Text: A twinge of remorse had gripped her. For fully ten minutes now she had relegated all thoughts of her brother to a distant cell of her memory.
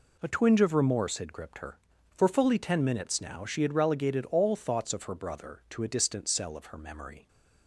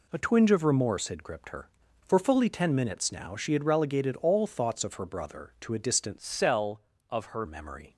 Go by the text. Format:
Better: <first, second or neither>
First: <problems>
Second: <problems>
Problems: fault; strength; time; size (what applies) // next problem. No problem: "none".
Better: first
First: none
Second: changes voice from "cell" to "her"; from 6.1 to 7.4 s; 1.3 s long